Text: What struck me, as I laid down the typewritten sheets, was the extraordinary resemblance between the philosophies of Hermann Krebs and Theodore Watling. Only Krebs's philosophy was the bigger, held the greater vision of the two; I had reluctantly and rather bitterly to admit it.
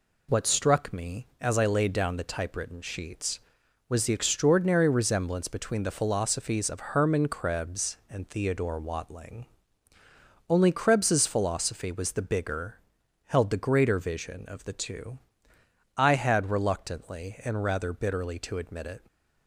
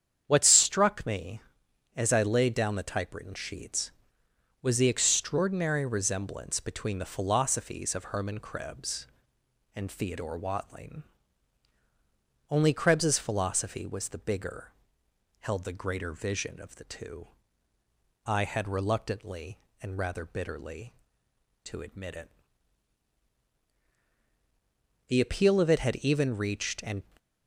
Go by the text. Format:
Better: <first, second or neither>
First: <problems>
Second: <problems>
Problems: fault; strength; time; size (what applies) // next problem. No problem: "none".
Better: first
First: none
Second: starts louder than the rest; strong; until 1.2 s; 8.5 dB // goes on to say "The appeal of it had even reached and"; strong; from 25.0 s on; 1.9 s long